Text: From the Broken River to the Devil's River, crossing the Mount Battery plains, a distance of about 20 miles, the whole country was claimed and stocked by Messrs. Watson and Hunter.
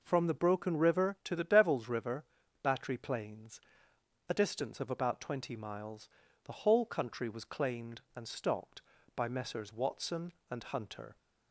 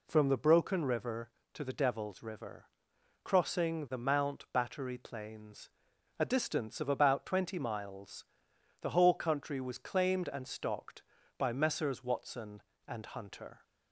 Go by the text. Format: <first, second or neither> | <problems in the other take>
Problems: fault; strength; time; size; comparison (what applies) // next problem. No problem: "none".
second | skips "crossing the Mount"; at 2.4 s